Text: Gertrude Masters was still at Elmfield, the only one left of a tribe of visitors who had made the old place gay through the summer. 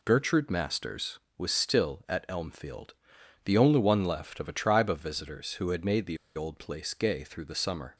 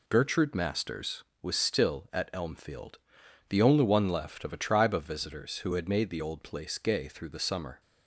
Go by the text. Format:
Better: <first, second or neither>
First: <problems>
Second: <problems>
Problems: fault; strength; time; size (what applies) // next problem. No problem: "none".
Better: second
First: pauses between "the" and "old"; slight; at 6.1 s; 0.18 s long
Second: none